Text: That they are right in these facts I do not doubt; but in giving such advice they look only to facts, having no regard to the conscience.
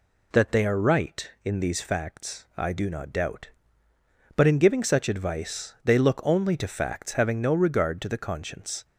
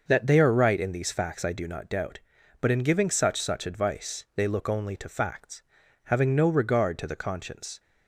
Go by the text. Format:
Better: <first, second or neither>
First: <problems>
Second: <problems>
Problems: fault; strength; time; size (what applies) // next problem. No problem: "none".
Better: first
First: none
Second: says "such" twice; at 3.4 s